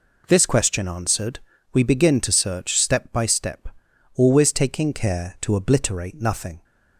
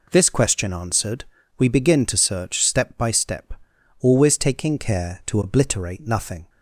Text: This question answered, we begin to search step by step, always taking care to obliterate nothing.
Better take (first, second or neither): neither